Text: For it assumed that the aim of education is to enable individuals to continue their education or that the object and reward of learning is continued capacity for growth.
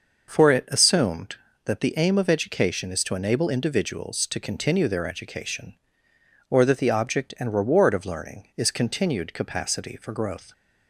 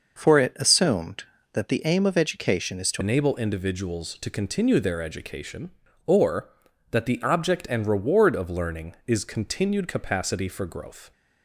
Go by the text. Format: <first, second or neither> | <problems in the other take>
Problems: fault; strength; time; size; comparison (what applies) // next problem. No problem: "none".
first | changes voice at "enable"; from 3.0 s on; 8.1 s long